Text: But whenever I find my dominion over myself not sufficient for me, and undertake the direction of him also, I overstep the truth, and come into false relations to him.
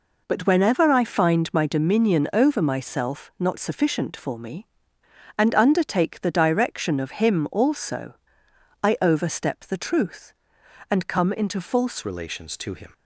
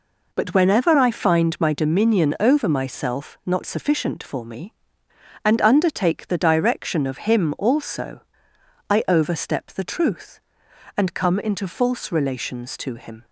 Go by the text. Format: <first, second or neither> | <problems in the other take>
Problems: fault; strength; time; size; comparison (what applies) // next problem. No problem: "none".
second | changes voice at "relations"; from 12.0 s on; 0.9 s long